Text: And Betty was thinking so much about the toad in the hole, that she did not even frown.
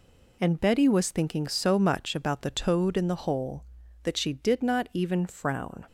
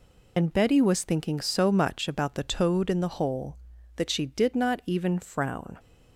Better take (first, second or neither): first